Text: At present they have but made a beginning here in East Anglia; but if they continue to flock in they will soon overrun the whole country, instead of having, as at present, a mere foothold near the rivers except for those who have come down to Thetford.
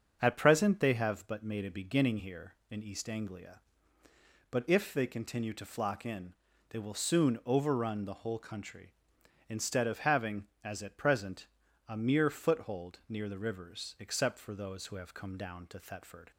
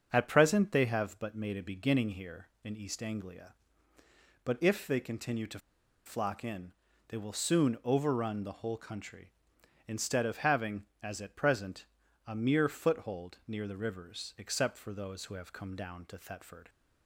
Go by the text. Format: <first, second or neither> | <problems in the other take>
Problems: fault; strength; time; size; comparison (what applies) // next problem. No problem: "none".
first | starts louder than the rest; until 1.1 s; 6.5 dB; also in the first // pauses between "to" and "flock"; noticeable; at 5.5 s; 0.47 s long // pauses between "in" and "they"; at 6.7 s; 0.38 s long; also in the first